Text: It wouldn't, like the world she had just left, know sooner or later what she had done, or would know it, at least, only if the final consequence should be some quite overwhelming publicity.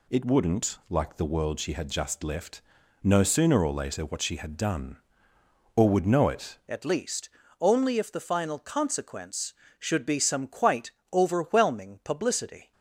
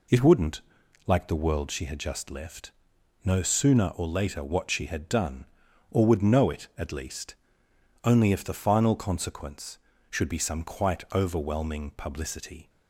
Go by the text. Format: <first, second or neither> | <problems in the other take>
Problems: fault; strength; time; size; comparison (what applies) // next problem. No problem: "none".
second | changes voice at "at"; from 6.6 s on; 6.1 s long // pauses between "quite" and "overwhelming"; slight; at 10.9 s; 0.20 s long